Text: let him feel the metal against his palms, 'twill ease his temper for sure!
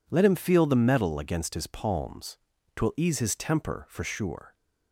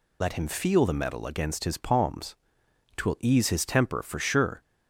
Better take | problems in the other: first | loses the start of "let"; at 0.2 s; 50 ms

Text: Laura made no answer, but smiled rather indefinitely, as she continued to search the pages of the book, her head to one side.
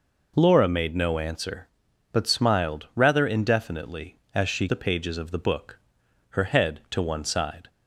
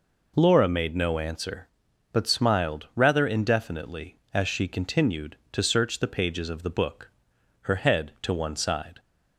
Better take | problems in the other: second | skips "continued to search"; at 4.6 s

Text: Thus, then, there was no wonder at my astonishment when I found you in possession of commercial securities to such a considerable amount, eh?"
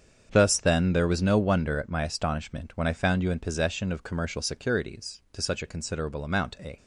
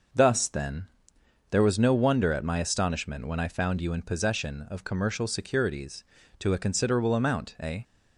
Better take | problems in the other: first | starts louder than the rest; noticeable; until 1.7 s; 6 dB; strong in the first // skips "such"; at 6.5 s

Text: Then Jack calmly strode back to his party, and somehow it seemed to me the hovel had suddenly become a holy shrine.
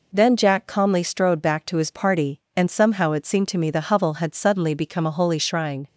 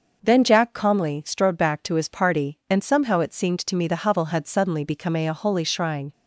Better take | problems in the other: first | starts louder than the rest; until 1.2 s; 6.5 dB // says "a" twice; at 5.2 s

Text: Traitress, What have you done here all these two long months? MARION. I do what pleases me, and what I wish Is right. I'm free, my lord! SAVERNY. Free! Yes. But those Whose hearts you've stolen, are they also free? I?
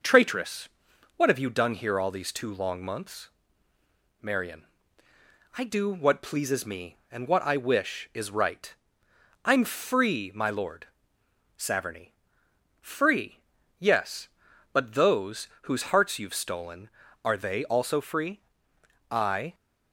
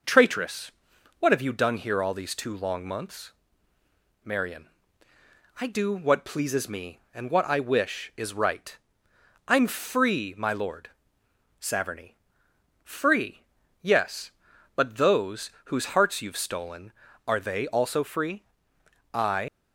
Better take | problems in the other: first | pauses between "those" and "Whose"; slight; at 15.4 s; 0.16 s long; slight in the first // leaves "I" unfinished; at 19.4 s; 85 ms

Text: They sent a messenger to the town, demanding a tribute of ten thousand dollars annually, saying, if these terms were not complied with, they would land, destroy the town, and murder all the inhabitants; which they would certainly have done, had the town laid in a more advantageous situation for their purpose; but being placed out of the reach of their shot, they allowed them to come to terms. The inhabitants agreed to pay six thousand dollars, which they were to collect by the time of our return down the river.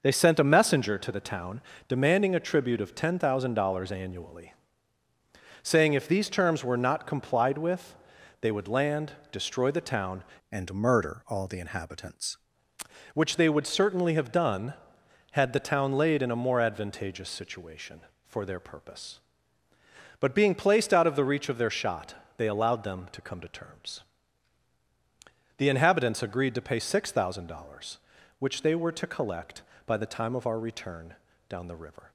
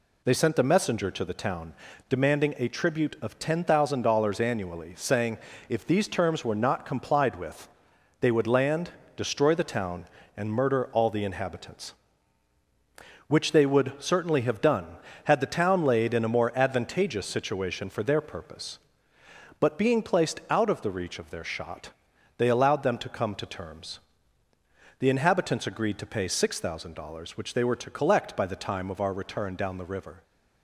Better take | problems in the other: second | changes voice from "and" to "inhabitants"; from 10.5 to 12.3 s; 1.8 s long // pauses between "return" and "down"; slight; at 31.1 s; 0.34 s long

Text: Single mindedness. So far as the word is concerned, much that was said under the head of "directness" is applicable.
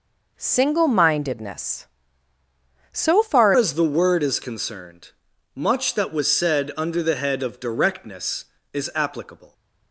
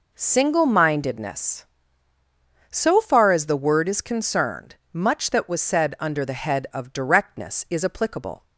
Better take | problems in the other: second | changes voice at "as"; from 3.5 s on; 6.0 s long

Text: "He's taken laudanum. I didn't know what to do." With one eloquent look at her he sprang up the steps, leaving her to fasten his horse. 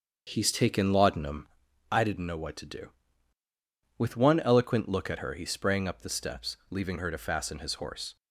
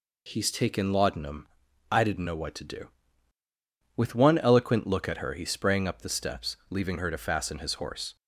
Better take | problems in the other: second | starts louder than the rest; until 1.7 s; 7 dB

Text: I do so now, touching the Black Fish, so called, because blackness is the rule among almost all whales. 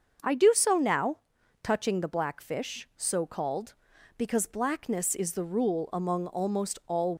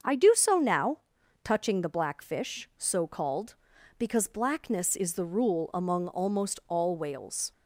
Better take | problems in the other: second | starts louder than the rest; until 1.7 s; 6.5 dB; also in the second // stops before "whales"; at 7.1 s

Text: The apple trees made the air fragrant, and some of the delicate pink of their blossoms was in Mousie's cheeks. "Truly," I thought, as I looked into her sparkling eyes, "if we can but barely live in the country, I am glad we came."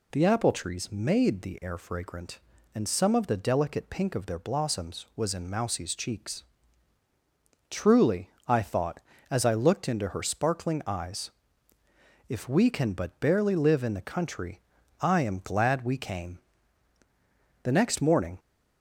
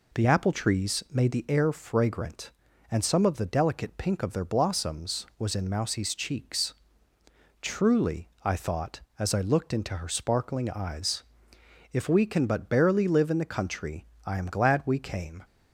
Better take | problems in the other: second | goes on to say "The next morning"; noticeable; from 17.6 s on; 0.76 s long

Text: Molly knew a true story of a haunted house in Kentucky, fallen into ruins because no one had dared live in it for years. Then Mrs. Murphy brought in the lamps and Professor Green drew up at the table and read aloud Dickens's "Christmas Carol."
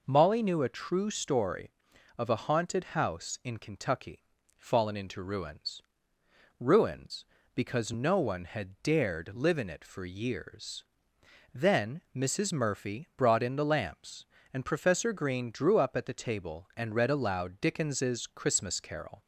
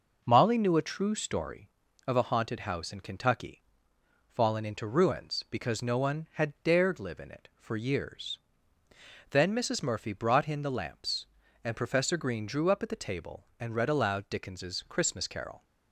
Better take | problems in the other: second | says "ruins" twice; at 6.5 s

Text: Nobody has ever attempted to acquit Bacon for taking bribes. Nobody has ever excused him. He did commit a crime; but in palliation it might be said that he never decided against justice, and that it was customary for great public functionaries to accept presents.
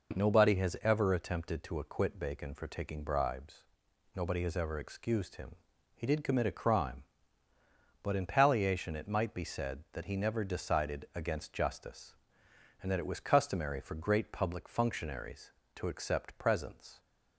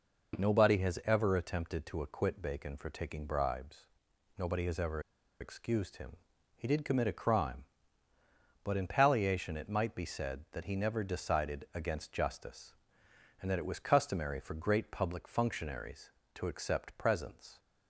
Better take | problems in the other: first | pauses between "ever" and "excused"; at 5.0 s; 0.40 s long

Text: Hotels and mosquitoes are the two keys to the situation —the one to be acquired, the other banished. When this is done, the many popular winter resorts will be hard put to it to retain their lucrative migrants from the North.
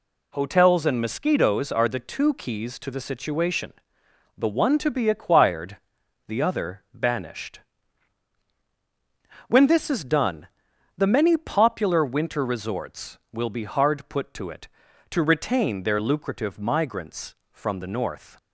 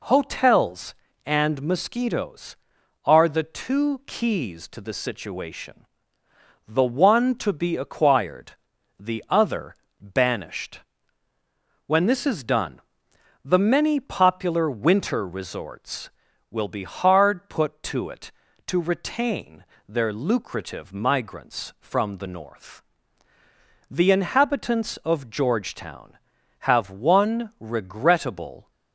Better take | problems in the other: first | pauses between "other" and "banished"; slight; at 9.7 s; 0.24 s long // pauses between "retain" and "their"; slight; at 19.6 s; 0.22 s long // goes on to say "The inhabitants of Georgetown have one regrettable"; strong; from 23.9 s on; 4.8 s long

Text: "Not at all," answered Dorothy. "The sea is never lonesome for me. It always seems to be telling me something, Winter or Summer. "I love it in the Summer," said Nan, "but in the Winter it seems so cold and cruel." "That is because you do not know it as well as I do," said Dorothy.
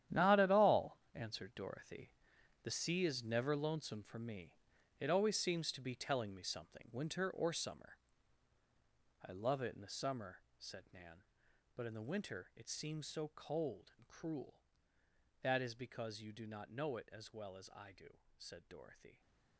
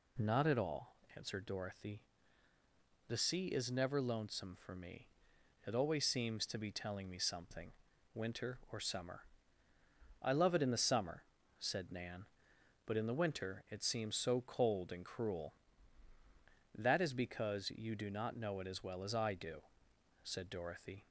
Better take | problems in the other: second | gets quieter; strong; throughout; 13.5 dB

